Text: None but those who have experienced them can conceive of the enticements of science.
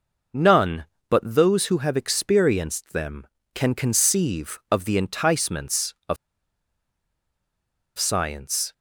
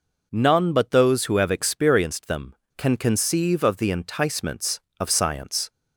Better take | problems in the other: second | pauses between "of" and "science"; strong; at 6.1 s; 1.8 s long

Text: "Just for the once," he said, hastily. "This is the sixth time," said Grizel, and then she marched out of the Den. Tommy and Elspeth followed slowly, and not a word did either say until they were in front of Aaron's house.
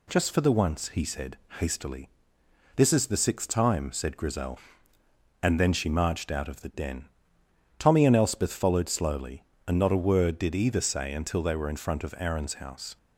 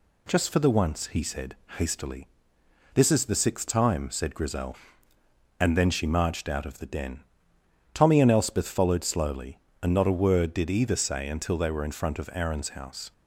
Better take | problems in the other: neither | none

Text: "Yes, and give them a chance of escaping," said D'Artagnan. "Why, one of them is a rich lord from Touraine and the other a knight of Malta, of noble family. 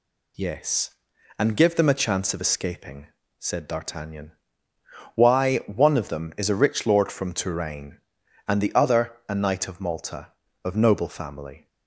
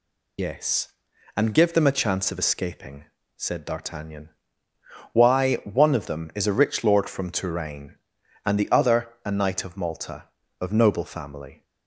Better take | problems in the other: first | loses the start of "Yes"; at 0.3 s; 45 ms

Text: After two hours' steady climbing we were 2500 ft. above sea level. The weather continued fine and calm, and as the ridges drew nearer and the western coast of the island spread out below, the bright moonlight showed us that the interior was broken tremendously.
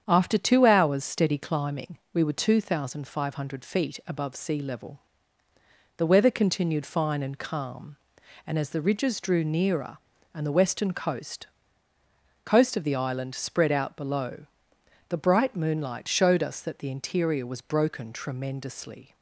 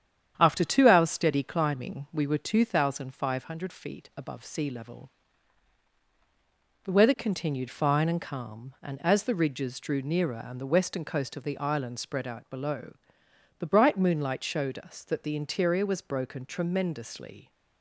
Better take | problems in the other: second | starts louder than the rest; strong; until 1.0 s; 8 dB; strong in the second // pauses between "climbing" and "we"; slight; at 1.9 s; 0.16 s long // says "coast" twice; at 12.4 s

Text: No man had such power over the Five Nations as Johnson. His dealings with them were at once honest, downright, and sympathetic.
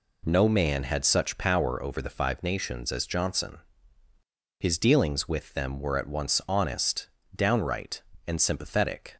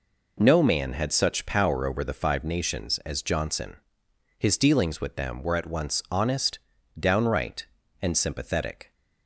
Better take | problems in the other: neither | none

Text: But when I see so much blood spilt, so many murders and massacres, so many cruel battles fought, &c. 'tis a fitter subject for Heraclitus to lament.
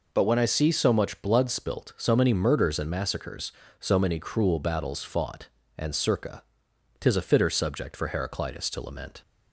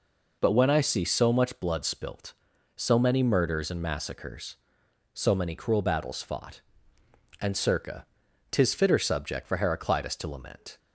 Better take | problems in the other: first | skips "a"; at 8.7 s

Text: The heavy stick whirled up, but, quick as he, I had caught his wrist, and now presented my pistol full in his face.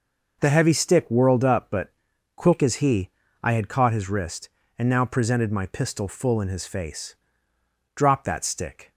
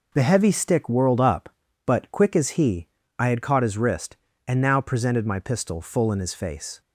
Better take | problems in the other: second | goes on to say "Drop that stick"; noticeable; from 7.9 s on; 0.96 s long

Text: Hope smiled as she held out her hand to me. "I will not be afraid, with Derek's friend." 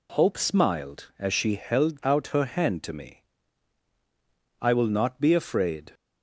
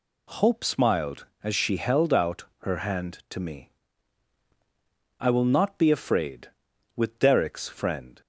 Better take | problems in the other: second | stops before "with Derek's friend"; at 5.9 s

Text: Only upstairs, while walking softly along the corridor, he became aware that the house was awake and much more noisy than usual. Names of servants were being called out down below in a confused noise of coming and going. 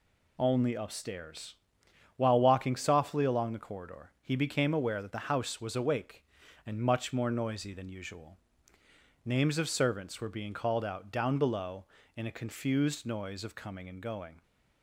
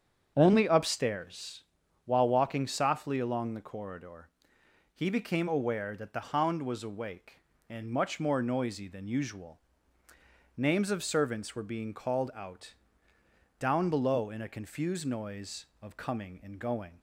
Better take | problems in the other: first | starts louder than the rest; strong; until 1.3 s; 8 dB // says "hound" for "house"; at 6.2 s // pauses between "out" and "down"; noticeable; at 12.7 s; 0.84 s long

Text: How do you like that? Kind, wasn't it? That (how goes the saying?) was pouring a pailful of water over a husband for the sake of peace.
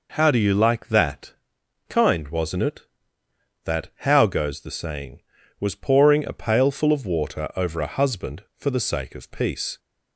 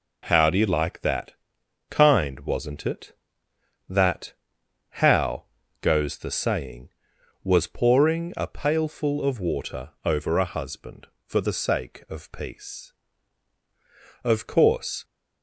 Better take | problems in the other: first | pauses between "how" and "goes"; at 5.4 s; 0.38 s long // goes on to say "Of course"; noticeable; from 14.2 s on; 0.80 s long

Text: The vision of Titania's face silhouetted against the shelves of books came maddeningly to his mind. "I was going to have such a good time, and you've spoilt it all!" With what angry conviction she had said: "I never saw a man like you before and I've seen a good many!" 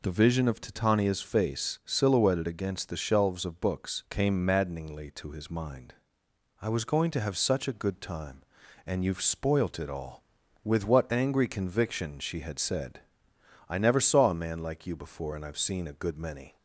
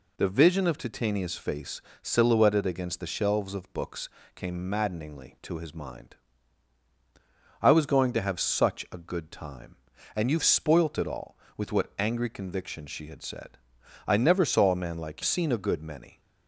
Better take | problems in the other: first | pauses between "face" and "silhouetted"; slight; at 1.8 s; 0.20 s long // pauses between "books" and "came"; slight; at 4.0 s; 0.28 s long // skips "you before and I've"; at 15.2 s

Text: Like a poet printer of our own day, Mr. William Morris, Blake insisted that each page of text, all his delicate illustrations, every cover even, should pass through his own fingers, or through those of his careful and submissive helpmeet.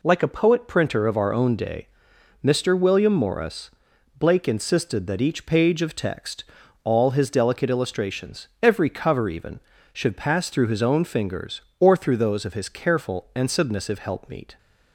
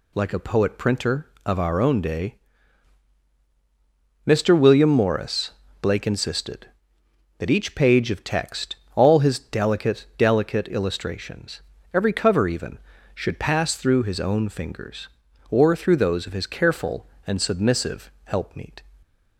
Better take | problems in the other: first | says "delicate" twice; at 10.1 s

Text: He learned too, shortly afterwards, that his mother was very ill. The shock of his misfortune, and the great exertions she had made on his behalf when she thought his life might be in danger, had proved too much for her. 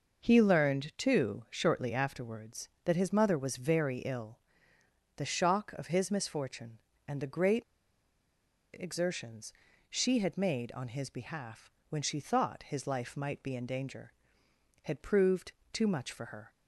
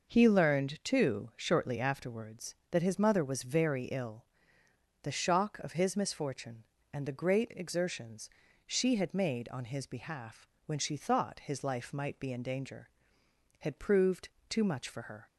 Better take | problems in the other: second | pauses between "great" and "exertions"; at 7.6 s; 1.0 s long // pauses between "exertions" and "she"; at 9.5 s; 0.38 s long; also in the second // pauses between "behalf" and "when"; slight; at 11.6 s; 0.20 s long; slight in the second // pauses between "proved" and "too"; slight; at 15.5 s; 0.20 s long; slight in the second

